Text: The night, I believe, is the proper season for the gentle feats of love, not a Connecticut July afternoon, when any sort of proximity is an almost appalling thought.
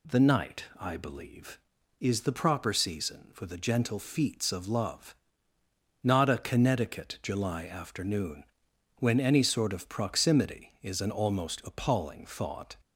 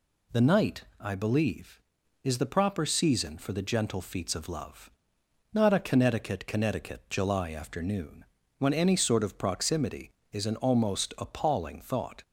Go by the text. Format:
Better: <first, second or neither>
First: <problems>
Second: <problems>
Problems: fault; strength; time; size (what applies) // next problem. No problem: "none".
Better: first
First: none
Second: says "Connecticut" twice; at 6.4 s